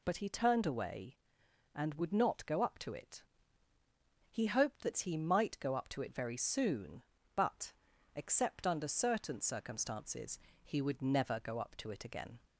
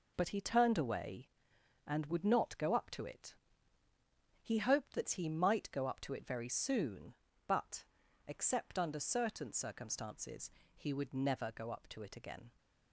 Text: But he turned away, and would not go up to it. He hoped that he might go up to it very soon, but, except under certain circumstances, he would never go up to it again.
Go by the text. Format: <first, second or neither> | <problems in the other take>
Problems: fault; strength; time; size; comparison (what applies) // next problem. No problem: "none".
first | gets quieter; strong; throughout; 8 dB